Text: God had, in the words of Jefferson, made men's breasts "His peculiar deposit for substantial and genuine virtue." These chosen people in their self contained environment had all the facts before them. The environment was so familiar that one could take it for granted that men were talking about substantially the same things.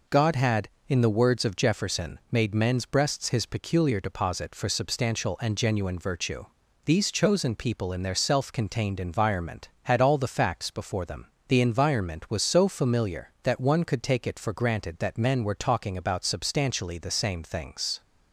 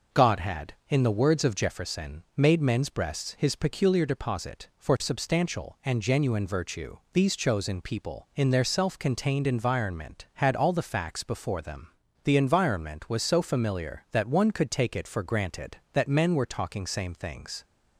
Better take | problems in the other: first | skips "about substantially the"; at 16.8 s

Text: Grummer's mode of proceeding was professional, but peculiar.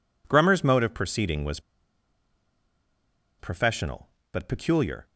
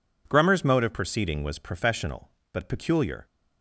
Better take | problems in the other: second | pauses between "was" and "professional"; strong; at 1.5 s; 1.7 s long

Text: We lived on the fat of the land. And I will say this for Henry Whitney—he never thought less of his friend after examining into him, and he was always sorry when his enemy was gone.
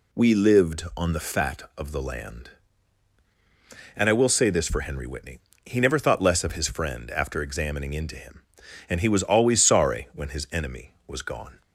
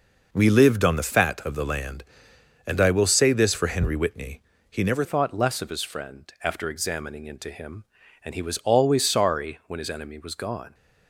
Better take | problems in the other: first | changes voice at "thought"; from 5.0 s on; 5.7 s long

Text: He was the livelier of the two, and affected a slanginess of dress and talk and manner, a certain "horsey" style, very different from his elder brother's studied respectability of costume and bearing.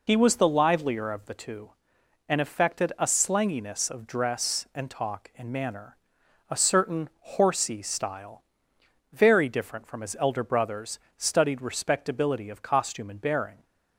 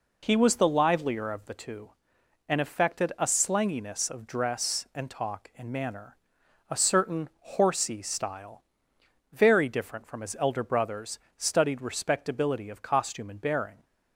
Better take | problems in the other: second | loses the start of "He"; at 0.0 s; 45 ms // pauses between "brother's" and "studied"; slight; at 10.9 s; 0.16 s long; slight in the second

